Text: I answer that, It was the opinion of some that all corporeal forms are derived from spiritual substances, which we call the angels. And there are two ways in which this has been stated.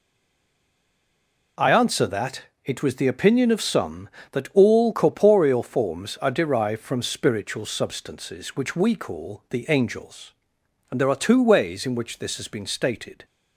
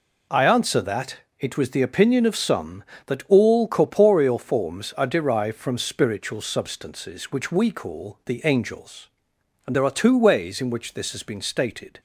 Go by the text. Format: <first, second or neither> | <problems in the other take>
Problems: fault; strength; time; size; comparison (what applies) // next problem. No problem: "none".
second | stays silent before the first word; noticeable; until 1.5 s; 1.5 s long